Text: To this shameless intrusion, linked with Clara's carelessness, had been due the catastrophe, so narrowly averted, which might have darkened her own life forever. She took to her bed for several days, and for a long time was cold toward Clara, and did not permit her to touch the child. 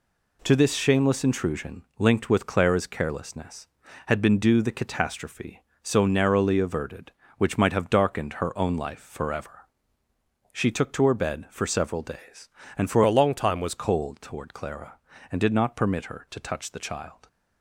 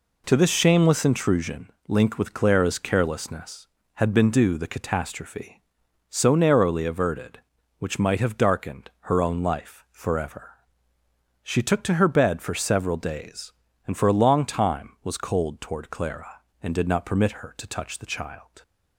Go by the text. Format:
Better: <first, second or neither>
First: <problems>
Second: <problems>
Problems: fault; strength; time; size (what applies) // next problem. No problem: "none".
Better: second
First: changes voice from "a" to "was"; from 13.0 to 13.7 s; 0.7 s long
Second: none